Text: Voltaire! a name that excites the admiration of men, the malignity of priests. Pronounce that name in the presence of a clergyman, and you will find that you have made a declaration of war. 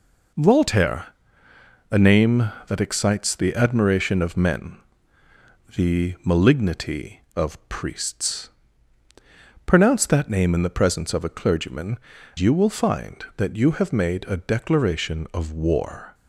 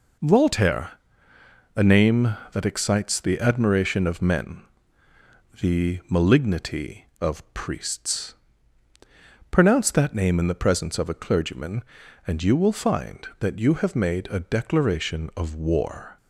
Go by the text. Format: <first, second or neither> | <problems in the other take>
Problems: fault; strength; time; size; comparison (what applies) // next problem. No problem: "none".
second | skips "and"; at 12.1 s